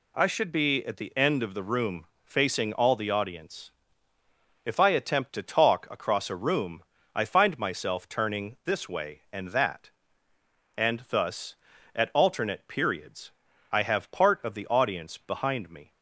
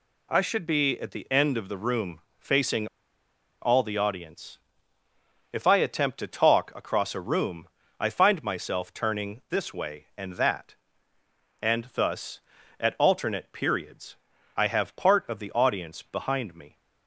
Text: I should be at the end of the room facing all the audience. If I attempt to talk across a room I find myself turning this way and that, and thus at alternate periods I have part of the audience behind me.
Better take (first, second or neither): first